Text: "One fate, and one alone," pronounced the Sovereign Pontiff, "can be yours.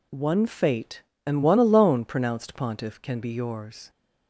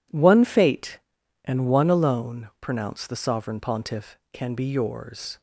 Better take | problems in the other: second | skips "the Sovereign"; at 2.5 s

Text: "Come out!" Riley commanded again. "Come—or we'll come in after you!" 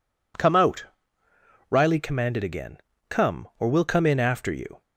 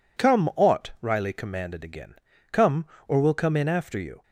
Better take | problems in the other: first | says "ought" for "out"; at 0.5 s

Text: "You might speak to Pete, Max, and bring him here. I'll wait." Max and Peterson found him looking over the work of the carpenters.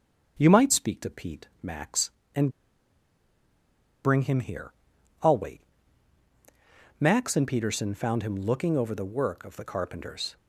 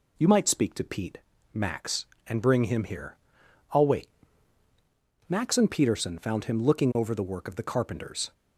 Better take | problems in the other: second | starts louder than the rest; strong; until 1.4 s; 7.5 dB // pauses between "and" and "bring"; strong; at 2.4 s; 1.5 s long

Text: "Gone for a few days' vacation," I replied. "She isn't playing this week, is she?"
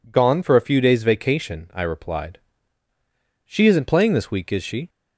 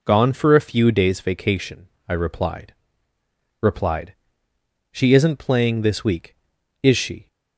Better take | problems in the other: first | says "replied" twice; at 3.6 s

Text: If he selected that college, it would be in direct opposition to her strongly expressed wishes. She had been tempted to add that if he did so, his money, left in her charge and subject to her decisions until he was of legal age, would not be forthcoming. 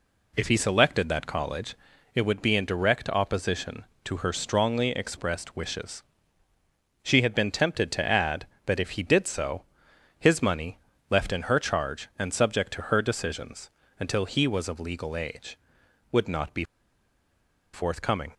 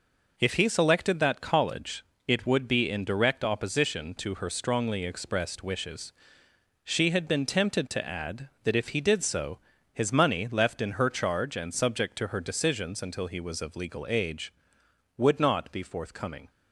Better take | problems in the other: second | pauses between "decisions" and "until"; slight; at 13.7 s; 0.28 s long // pauses between "be" and "forthcoming"; at 16.6 s; 1.0 s long

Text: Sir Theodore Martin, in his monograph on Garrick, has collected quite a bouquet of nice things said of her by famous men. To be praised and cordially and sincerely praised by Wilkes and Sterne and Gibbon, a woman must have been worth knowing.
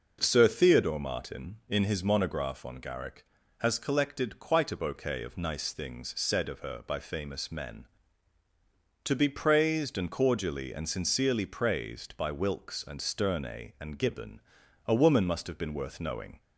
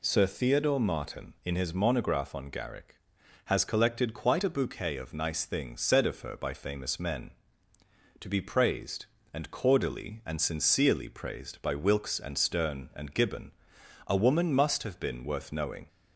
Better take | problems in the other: neither | none

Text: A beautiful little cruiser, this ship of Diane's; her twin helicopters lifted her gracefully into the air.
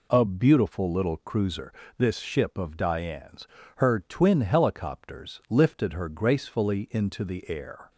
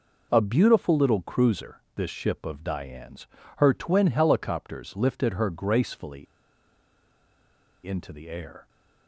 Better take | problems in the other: first | pauses between "gracefully" and "into"; strong; at 6.2 s; 1.6 s long

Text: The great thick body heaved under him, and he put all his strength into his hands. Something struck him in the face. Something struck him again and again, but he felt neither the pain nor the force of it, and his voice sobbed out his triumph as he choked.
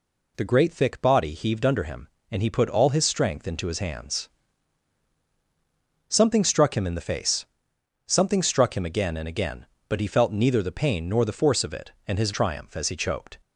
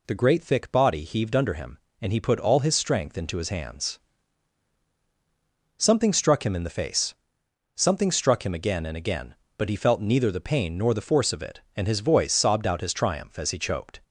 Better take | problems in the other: second | skips "voice sobbed out his"; at 12.3 s

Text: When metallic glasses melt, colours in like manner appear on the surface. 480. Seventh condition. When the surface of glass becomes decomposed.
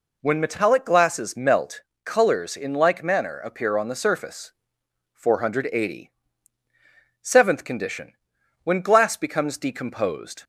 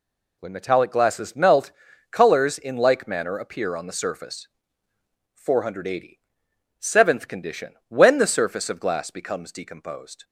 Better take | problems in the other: second | skips "the surface of"; at 8.8 s

